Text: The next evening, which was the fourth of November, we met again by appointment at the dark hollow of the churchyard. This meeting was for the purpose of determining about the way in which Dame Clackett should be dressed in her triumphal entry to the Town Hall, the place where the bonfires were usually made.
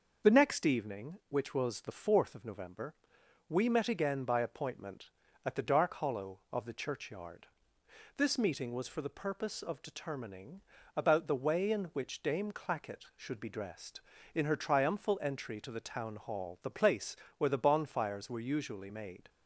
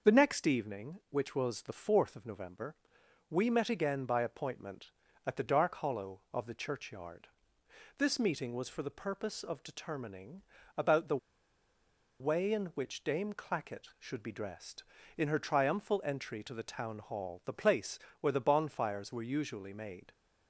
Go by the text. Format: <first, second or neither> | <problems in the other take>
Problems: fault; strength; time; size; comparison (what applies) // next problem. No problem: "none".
first | pauses between "determining" and "about"; slight; at 10.4 s; 0.36 s long; slight in the first // pauses between "the" and "way"; at 11.1 s; 1.0 s long // pauses between "place" and "where"; slight; at 17.9 s; 0.22 s long; slight in the first